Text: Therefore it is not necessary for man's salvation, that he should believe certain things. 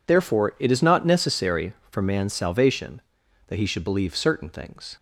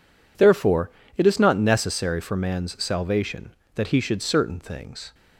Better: first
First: none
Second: pauses between "Therefore" and "it"; slight; at 0.8 s; 0.26 s long // skips "believe"; at 4.2 s

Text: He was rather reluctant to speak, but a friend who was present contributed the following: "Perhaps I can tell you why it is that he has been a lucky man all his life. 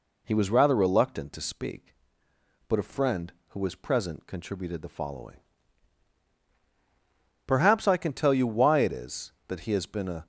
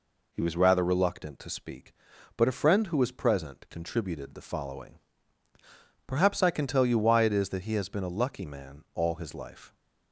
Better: second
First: stops before "lucky man all his life"; at 10.2 s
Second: none

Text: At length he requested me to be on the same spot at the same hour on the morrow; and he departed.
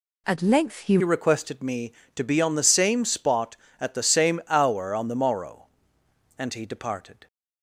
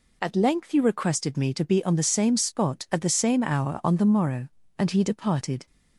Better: second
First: changes voice at "requested"; from 1.0 s on; 6.2 s long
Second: none

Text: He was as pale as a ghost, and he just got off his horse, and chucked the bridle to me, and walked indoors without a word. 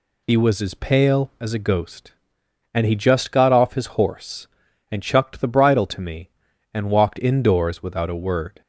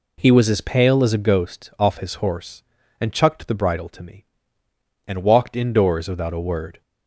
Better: first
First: none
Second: skips "and he just got"; at 1.7 s

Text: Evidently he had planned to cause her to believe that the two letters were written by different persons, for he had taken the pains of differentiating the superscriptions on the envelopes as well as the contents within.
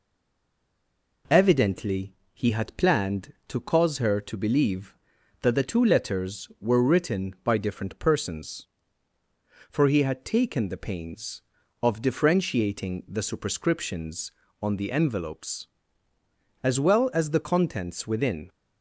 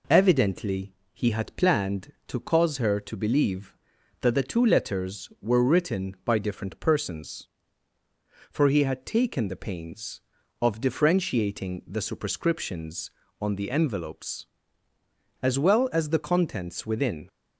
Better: second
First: stays silent before the first word; noticeable; until 1.2 s; 1.2 s long // pauses between "Evidently" and "he"; slight; at 2.1 s; 0.18 s long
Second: pauses between "Evidently" and "he"; slight; at 0.9 s; 0.18 s long

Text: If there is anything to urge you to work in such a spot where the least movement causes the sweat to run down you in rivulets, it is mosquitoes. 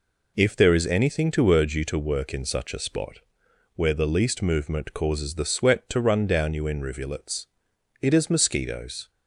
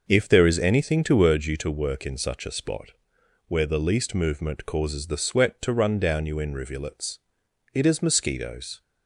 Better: first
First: pauses between "spot" and "where"; noticeable; at 3.1 s; 0.58 s long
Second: starts louder than the rest; noticeable; until 1.4 s; 6 dB // pauses between "spot" and "where"; noticeable; at 2.9 s; 0.58 s long

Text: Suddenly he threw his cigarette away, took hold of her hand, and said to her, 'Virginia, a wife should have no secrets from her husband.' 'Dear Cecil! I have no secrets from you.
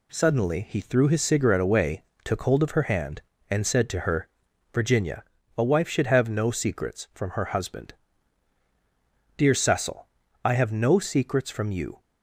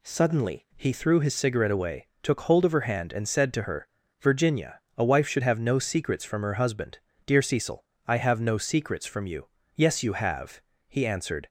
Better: first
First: none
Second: goes on to say "Yes you have he answered"; strong; from 9.7 s on; 1.7 s long

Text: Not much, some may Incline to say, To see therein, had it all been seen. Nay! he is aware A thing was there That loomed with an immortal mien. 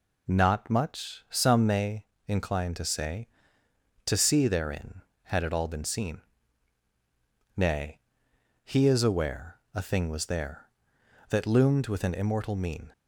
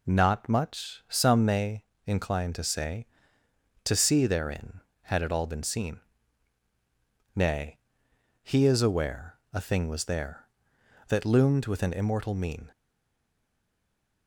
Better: first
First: pauses between "may" and "Incline"; slight; at 2.0 s; 0.22 s long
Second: pauses between "may" and "Incline"; slight; at 1.8 s; 0.22 s long // stays silent after the last word; noticeable; from 12.7 s on; 1.5 s long

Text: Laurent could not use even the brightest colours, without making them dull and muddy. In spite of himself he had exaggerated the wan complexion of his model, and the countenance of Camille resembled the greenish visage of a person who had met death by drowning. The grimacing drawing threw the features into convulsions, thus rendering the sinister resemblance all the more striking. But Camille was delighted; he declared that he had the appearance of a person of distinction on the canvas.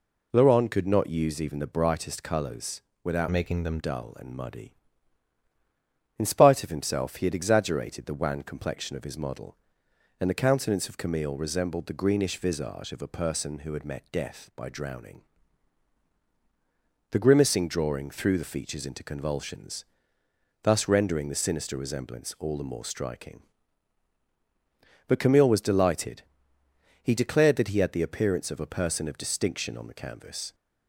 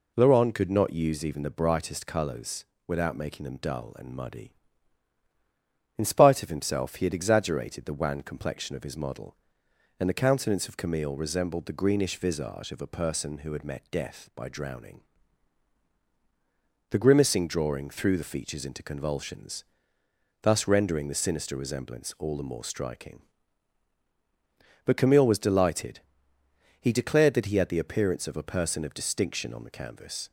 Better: second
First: changes voice from "making" to "them"; from 3.2 to 3.7 s; 0.5 s long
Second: none

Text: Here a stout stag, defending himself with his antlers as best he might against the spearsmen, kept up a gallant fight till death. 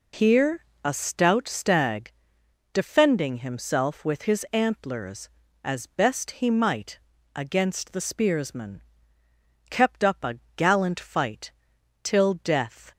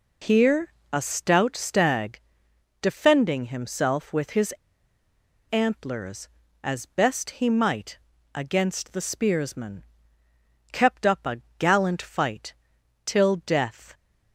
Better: first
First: pauses between "Here" and "a"; slight; at 0.6 s; 0.20 s long // pauses between "might" and "against"; slight; at 7.0 s; 0.34 s long // pauses between "a" and "gallant"; slight; at 10.3 s; 0.18 s long // pauses between "fight" and "till"; noticeable; at 11.5 s; 0.52 s long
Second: pauses between "Here" and "a"; slight; at 0.7 s; 0.20 s long // pauses between "his" and "antlers"; noticeable; at 4.5 s; 0.97 s long // pauses between "might" and "against"; slight; at 7.9 s; 0.34 s long // pauses between "a" and "gallant"; slight; at 11.4 s; 0.18 s long // pauses between "fight" and "till"; noticeable; at 12.5 s; 0.52 s long

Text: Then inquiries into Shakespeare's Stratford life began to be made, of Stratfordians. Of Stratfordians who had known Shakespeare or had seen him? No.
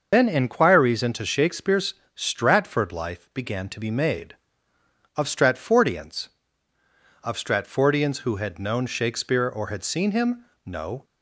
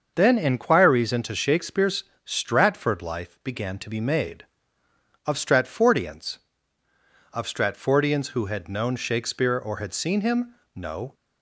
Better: second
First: loses the start of "Then"; at 0.1 s; 65 ms // starts louder than the rest; until 1.1 s; 6 dB // pauses between "Shakespeare's" and "Stratford"; slight; at 1.9 s; 0.20 s long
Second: starts louder than the rest; until 1.1 s; 6.5 dB // pauses between "Shakespeare's" and "Stratford"; slight; at 2.0 s; 0.20 s long

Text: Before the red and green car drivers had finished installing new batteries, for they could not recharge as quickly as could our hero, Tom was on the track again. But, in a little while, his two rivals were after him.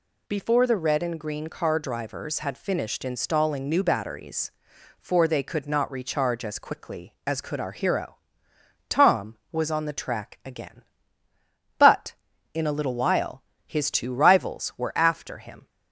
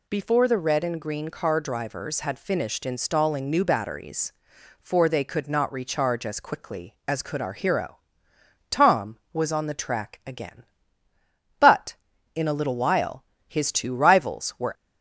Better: first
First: none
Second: stops before "after him"; at 14.7 s

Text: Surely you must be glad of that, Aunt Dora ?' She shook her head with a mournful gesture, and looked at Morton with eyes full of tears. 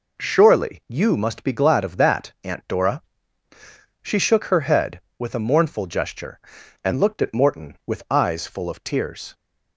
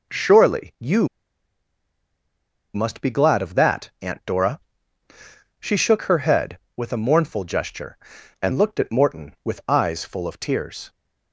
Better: first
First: none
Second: pauses between "you" and "must"; strong; at 1.0 s; 1.6 s long

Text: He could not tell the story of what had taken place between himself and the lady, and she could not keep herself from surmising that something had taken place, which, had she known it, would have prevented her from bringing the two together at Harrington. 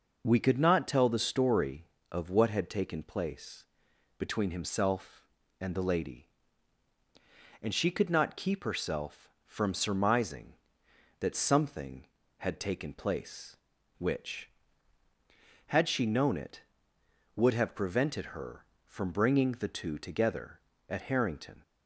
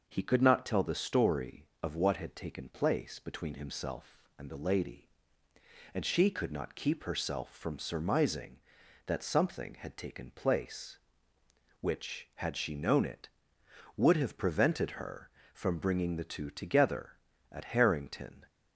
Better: second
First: says "We" for "He"; at 0.2 s // pauses between "place" and "between"; noticeable; at 3.6 s; 0.54 s long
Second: none

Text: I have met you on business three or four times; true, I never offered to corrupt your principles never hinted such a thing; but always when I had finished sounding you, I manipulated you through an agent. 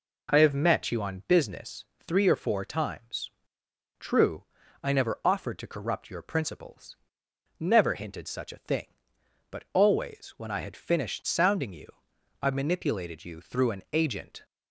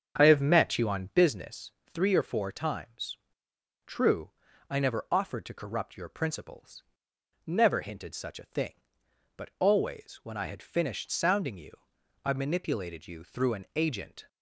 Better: first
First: pauses between "business" and "three"; slight; at 1.8 s; 0.20 s long // pauses between "principles" and "never"; noticeable; at 6.9 s; 0.64 s long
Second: starts louder than the rest; strong; until 1.3 s; 7.5 dB // pauses between "business" and "three"; slight; at 1.7 s; 0.20 s long // pauses between "principles" and "never"; noticeable; at 6.8 s; 0.64 s long

